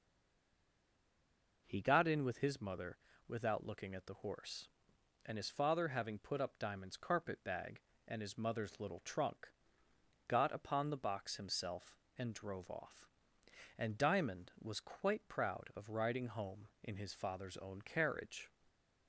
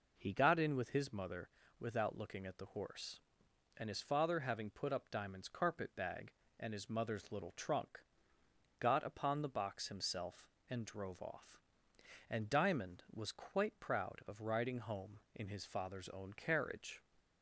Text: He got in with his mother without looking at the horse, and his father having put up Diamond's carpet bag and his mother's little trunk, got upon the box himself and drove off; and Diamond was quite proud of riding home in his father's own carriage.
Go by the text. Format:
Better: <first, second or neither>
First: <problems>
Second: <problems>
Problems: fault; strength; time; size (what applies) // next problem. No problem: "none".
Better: second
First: stays silent before the first word; noticeable; until 1.6 s; 1.6 s long // pauses between "mother" and "without"; slight; at 2.9 s; 0.30 s long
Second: pauses between "mother" and "without"; slight; at 1.4 s; 0.30 s long